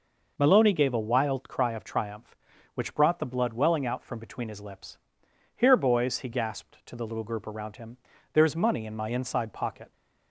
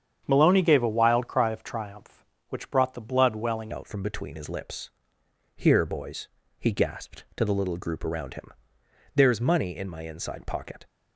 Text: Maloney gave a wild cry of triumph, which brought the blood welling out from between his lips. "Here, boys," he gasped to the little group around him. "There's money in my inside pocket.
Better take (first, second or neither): first